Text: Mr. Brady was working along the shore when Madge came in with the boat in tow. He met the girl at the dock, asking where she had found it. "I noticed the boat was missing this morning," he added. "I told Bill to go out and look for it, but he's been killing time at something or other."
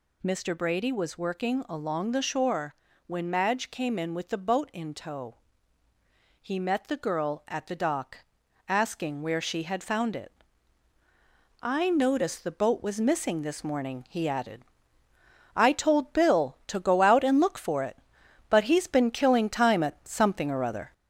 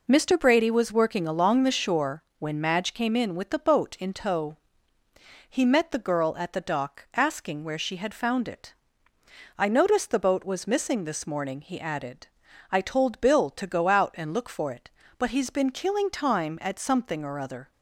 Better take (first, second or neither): second